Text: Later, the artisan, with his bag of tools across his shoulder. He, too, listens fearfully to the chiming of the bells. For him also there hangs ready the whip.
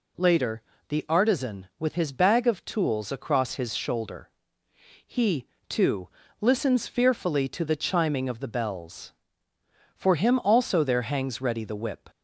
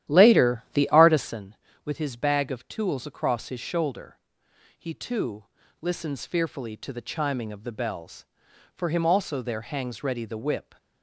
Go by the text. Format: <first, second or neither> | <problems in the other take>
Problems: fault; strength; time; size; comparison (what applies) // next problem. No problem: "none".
first | starts louder than the rest; strong; until 1.4 s; 12 dB